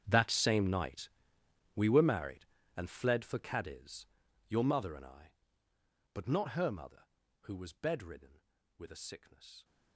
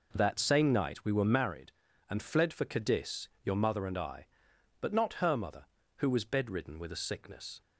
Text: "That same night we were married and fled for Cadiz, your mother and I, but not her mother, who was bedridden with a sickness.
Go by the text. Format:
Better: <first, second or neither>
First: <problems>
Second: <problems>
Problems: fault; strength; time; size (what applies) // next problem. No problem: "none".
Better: second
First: gets quieter; strong; throughout; 20.5 dB // pauses between "night" and "we"; noticeable; at 1.0 s; 0.66 s long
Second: none